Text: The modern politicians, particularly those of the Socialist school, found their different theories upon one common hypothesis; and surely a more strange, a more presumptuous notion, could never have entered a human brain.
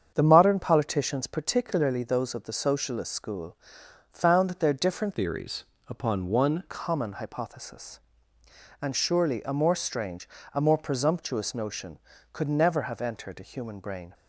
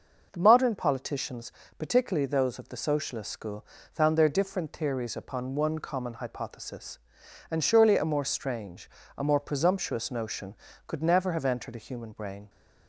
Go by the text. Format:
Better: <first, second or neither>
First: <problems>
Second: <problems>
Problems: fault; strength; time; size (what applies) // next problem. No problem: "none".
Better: second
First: starts louder than the rest; strong; until 1.1 s; 7.5 dB // changes voice from "theories" to "one"; from 5.1 to 6.6 s; 1.5 s long // pauses between "theories" and "upon"; slight; at 5.6 s; 0.24 s long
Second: starts louder than the rest; noticeable; until 1.3 s; 6 dB